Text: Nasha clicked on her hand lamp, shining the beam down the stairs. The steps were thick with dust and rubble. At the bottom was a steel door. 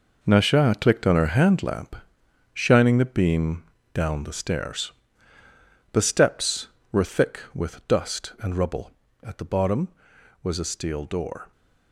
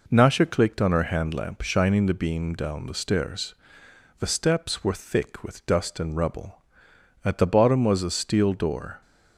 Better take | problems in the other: second | gets quieter; strong; throughout; 10.5 dB // pauses between "beam" and "down"; slight; at 3.6 s; 0.30 s long

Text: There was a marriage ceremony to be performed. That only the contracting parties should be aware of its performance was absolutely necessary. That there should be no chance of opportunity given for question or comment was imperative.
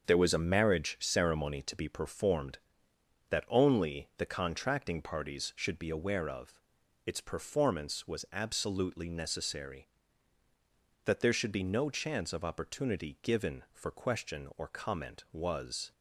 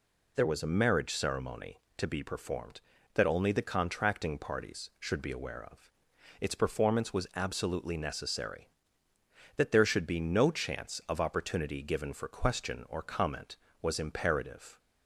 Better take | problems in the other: second | starts louder than the rest; until 1.0 s; 6.5 dB // pauses between "of" and "its"; noticeable; at 6.5 s; 0.46 s long; noticeable in the second // stops before "imperative"; at 15.9 s

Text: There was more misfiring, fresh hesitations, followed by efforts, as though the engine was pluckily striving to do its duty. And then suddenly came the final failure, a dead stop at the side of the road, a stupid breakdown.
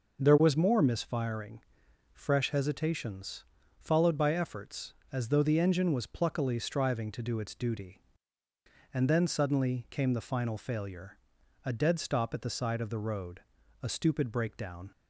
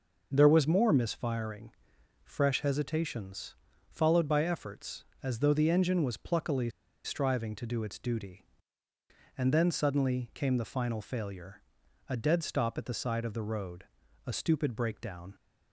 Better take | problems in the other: first | pauses between "pluckily" and "striving"; slight; at 6.6 s; 0.34 s long

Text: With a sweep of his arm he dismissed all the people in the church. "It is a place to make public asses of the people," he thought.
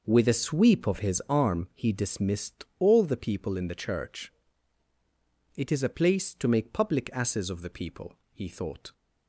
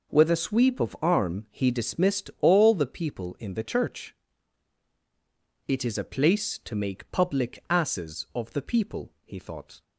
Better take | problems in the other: first | skips "his"; at 0.9 s

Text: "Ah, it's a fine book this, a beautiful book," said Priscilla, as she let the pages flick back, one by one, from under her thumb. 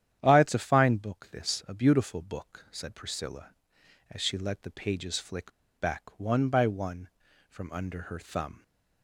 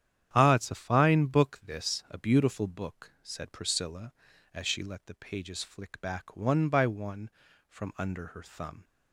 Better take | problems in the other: second | starts louder than the rest; strong; until 1.2 s; 10 dB; strong in the second // pauses between "flick" and "back"; slight; at 5.5 s; 0.25 s long

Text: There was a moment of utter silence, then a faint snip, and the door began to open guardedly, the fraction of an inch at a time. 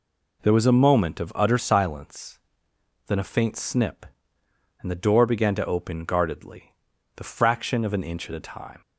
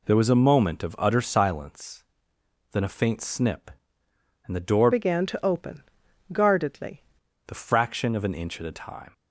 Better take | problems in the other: first | changes voice from "began" to "guardedly"; from 4.9 to 7.0 s; 2.1 s long // pauses between "open" and "guardedly"; noticeable; at 5.8 s; 0.50 s long

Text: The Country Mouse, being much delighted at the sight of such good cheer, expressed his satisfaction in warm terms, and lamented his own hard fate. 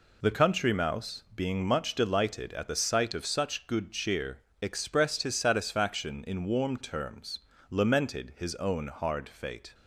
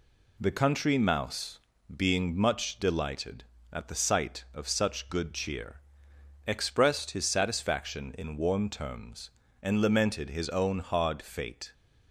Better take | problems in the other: second | skips "and"; at 7.5 s

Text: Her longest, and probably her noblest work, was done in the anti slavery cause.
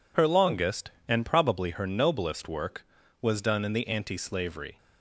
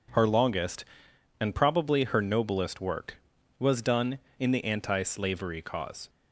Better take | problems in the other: second | stops before "cause"; at 4.7 s

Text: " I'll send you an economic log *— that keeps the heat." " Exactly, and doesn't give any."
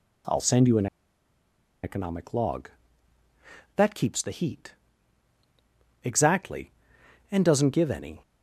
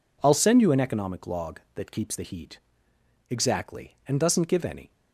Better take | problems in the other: second | pauses between "an" and "economic"; noticeable; at 0.8 s; 0.97 s long

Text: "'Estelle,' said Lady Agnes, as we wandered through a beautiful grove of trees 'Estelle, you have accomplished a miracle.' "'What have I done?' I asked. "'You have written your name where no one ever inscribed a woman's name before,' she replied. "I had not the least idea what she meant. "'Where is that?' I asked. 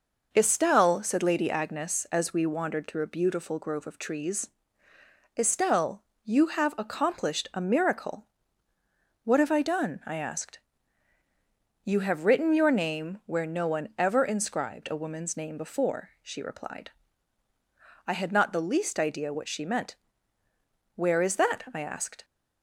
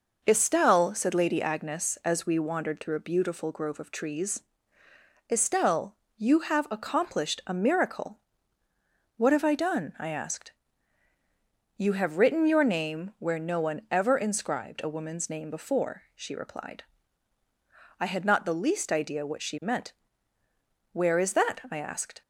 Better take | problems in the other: neither | pauses between "trees" and "Estelle"; noticeable; the same in both

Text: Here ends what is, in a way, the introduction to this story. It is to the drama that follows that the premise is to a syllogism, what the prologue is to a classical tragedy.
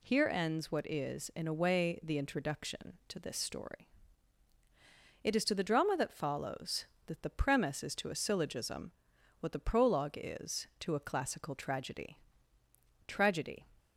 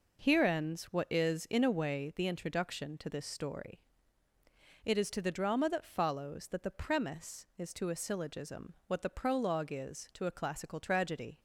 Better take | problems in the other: second | says "tragedy" twice; at 13.0 s

